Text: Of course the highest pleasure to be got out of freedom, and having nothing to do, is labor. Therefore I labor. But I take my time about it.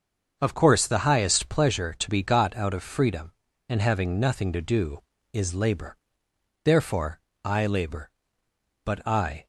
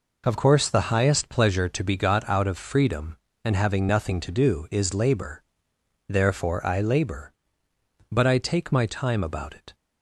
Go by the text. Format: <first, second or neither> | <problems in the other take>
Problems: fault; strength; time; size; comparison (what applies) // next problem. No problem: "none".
second | starts louder than the rest; until 1.4 s; 6.5 dB // pauses between "Therefore" and "I"; slight; at 7.2 s; 0.24 s long // stops before "take my time about it"; at 9.4 s